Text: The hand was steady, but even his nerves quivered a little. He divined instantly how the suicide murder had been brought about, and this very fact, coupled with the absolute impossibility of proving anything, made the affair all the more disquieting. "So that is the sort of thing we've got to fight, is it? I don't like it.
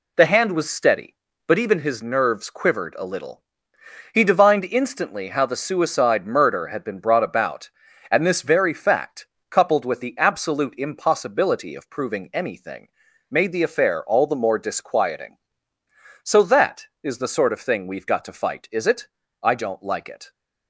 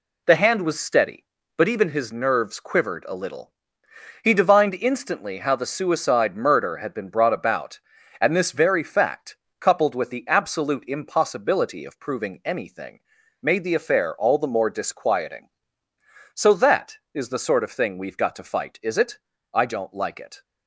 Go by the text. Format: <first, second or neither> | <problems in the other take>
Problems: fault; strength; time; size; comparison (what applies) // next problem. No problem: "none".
neither | none